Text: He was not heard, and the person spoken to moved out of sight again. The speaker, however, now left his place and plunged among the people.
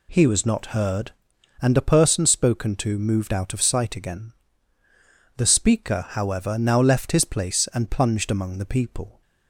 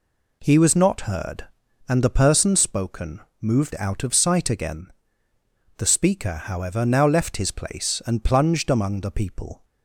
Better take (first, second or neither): first